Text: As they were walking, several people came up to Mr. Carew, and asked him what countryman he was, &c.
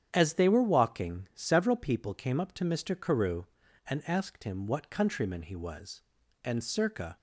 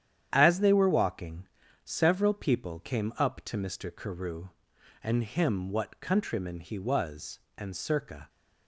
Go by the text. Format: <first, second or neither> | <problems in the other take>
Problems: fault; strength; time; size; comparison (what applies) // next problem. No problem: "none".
first | starts louder than the rest; strong; until 1.3 s; 10 dB; strong in the first // skips "asked"; at 5.2 s